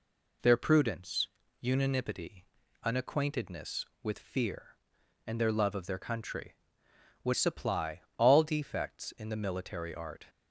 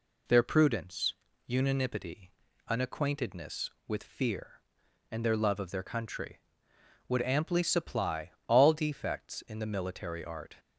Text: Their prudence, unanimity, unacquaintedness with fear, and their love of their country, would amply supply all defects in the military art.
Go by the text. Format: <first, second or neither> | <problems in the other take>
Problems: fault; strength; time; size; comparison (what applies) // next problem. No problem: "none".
second | skips "amply"; at 7.3 s // pauses between "supply" and "all"; slight; at 8.0 s; 0.16 s long; slight in the second